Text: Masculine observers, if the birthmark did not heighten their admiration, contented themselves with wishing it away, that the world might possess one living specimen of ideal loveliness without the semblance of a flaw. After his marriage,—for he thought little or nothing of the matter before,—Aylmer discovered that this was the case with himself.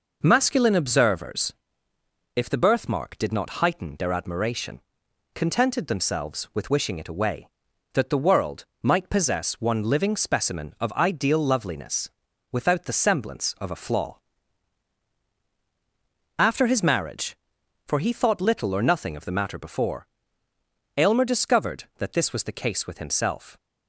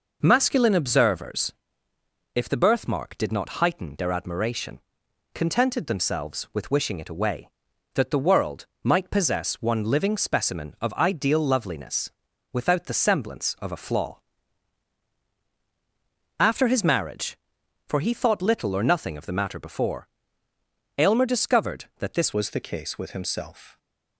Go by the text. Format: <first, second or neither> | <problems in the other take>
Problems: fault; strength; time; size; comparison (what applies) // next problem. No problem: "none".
first | pauses between "world" and "might"; slight; at 8.6 s; 0.16 s long; slight in the first // pauses between "loveliness" and "without"; at 12.1 s; 0.42 s long; also in the first // changes voice at "was"; from 22.3 s on; 1.4 s long